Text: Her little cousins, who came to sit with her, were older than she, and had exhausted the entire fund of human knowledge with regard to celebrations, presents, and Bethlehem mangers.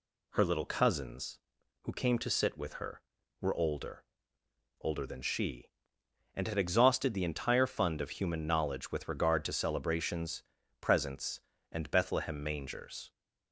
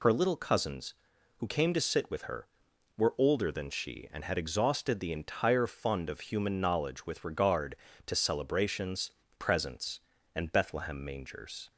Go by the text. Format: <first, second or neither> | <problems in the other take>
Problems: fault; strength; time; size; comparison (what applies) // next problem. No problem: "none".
second | says "older" twice; at 4.8 s